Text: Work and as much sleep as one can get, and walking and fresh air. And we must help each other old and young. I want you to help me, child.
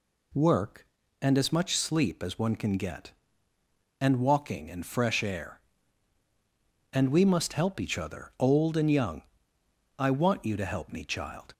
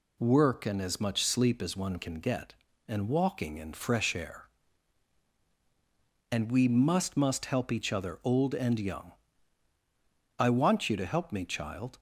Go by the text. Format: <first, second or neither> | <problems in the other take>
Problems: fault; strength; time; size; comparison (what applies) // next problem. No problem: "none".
first | says "must" twice; at 7.1 s